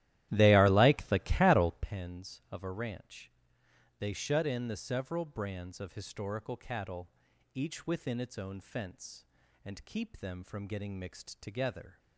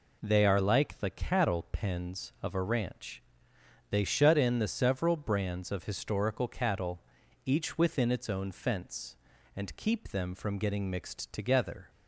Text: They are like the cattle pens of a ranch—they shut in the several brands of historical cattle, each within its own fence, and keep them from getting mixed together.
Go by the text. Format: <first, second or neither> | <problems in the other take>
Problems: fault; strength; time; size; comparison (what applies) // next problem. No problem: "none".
second | starts louder than the rest; strong; until 1.9 s; 14 dB